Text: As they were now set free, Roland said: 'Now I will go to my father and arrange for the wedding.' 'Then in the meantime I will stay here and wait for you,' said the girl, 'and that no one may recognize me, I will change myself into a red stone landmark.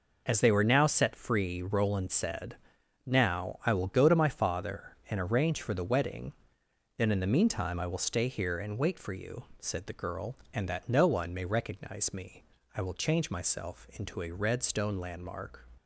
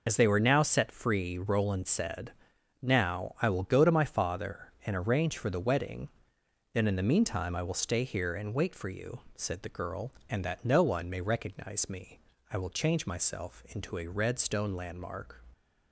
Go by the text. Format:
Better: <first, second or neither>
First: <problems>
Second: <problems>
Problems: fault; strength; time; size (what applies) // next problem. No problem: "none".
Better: first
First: none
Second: loses the start of "As"; at 0.0 s; 55 ms